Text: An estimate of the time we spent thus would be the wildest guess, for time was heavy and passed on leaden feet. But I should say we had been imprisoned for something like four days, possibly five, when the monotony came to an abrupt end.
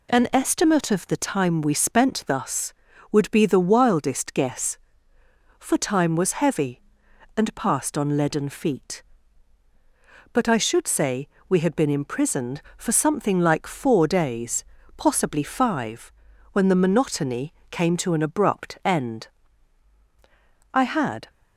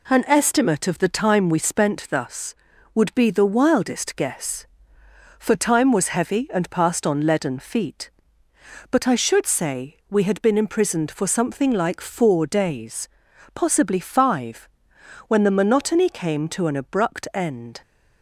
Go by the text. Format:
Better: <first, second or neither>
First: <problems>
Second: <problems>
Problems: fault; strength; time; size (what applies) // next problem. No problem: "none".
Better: second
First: pauses between "say" and "we"; slight; at 11.2 s; 0.20 s long // pauses between "monotony" and "came"; slight; at 17.5 s; 0.16 s long // goes on to say "I had"; from 20.7 s on; 0.56 s long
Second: none